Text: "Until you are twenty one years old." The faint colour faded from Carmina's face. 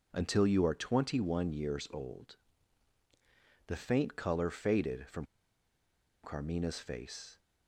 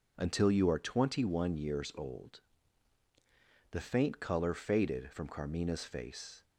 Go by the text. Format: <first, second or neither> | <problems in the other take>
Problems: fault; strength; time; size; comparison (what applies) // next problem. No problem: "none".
second | pauses between "from" and "Carmina's"; at 5.2 s; 0.99 s long